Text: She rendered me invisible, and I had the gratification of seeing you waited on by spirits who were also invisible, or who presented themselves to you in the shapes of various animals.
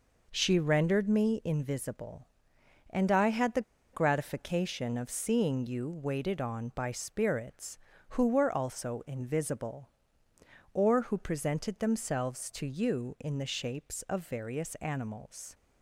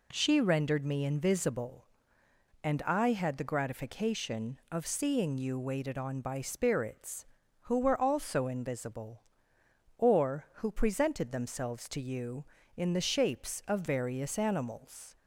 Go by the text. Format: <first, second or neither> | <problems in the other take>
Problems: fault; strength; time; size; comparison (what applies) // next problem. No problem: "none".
second | pauses between "the" and "gratification"; slight; at 3.6 s; 0.31 s long